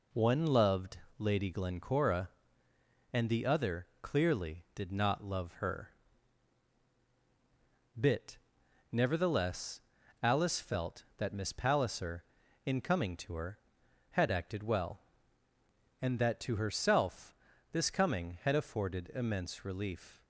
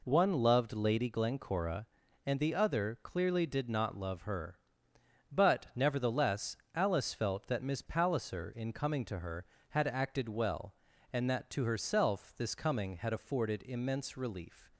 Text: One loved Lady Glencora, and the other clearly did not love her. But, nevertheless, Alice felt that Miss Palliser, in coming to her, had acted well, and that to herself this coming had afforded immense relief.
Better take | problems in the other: second | pauses between "loved" and "Lady"; slight; at 0.9 s; 0.22 s long // pauses between "other" and "clearly"; slight; at 3.8 s; 0.16 s long // says "Bit" for "But"; at 7.9 s // pauses between "herself" and "this"; slight; at 17.3 s; 0.36 s long

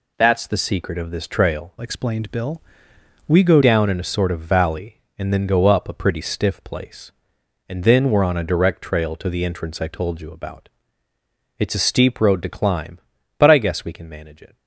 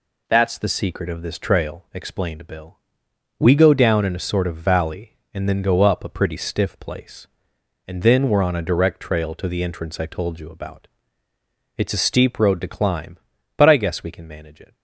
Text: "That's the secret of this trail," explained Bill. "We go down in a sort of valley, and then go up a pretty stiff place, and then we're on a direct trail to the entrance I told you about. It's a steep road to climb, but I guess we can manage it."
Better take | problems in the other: second | changes voice from "explained" to "go"; from 1.8 to 3.6 s; 1.8 s long

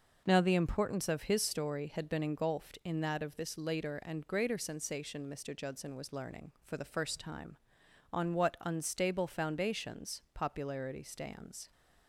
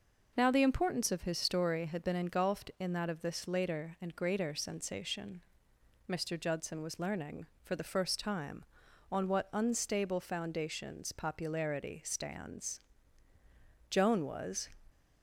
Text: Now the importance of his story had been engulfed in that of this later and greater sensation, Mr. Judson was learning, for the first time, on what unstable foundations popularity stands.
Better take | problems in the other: first | goes on to say "Joan was"; noticeable; from 13.9 s on; 0.78 s long

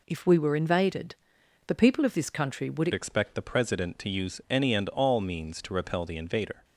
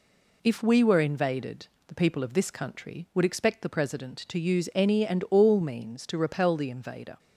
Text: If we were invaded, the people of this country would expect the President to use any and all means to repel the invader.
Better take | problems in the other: second | changes voice at "expect"; from 2.9 s on; 3.7 s long

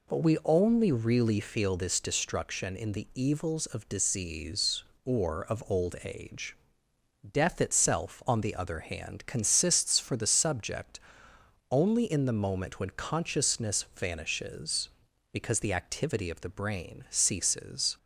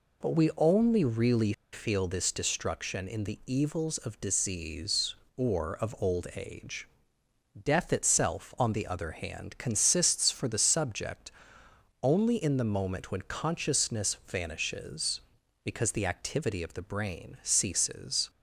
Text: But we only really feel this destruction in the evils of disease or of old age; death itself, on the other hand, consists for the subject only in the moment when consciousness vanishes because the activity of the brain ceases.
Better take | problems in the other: first | pauses between "really" and "feel"; slight; at 1.5 s; 0.21 s long // pauses between "subject" and "only"; noticeable; at 11.2 s; 0.72 s long; noticeable in the first

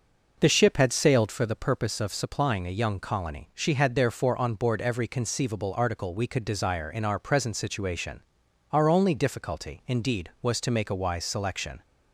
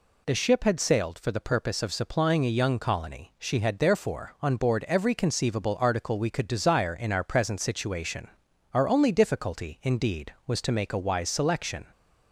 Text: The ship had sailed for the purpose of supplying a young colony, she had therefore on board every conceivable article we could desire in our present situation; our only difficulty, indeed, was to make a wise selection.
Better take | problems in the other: second | starts louder than the rest; noticeable; until 1.3 s; 5.5 dB

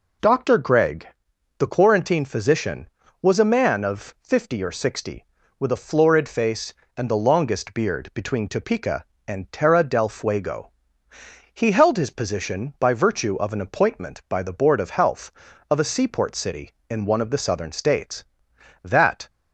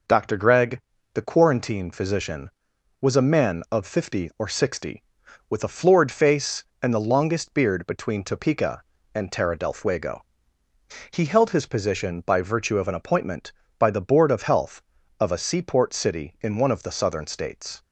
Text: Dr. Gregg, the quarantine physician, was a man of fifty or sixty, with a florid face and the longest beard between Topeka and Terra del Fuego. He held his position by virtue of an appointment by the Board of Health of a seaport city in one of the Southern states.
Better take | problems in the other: second | goes on to say "That"; slight; from 18.8 s on; 0.46 s long

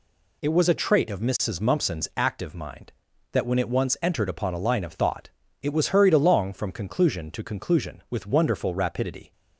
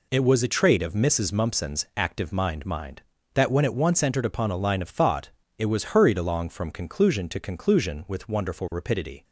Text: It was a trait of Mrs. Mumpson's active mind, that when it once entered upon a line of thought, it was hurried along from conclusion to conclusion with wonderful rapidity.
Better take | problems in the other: first | says "mind" twice; at 2.6 s

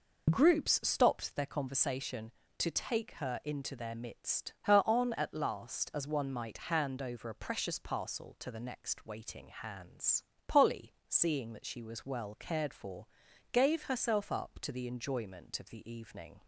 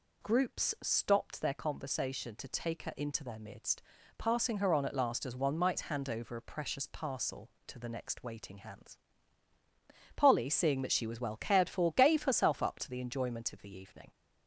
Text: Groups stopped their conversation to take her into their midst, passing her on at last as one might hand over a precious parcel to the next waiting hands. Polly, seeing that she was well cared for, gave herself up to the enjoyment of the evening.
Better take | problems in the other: second | skips "passing"; at 4.5 s

